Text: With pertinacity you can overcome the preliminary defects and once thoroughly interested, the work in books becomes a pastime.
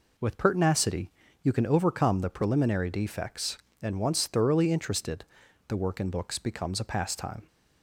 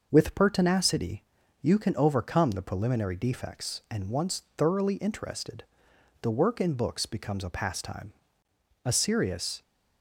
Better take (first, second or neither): first